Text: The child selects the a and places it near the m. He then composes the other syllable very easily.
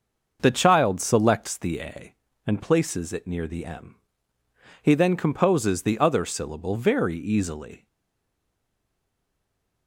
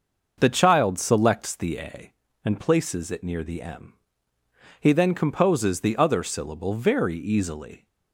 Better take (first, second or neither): second